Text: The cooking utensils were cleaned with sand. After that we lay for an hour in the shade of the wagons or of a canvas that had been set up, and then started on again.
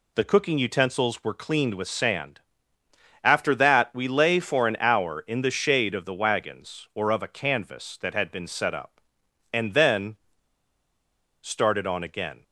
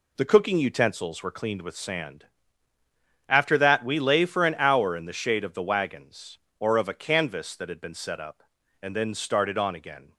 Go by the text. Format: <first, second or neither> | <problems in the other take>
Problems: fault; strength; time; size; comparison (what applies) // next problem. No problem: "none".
second | pauses between "then" and "started"; at 10.1 s; 1.2 s long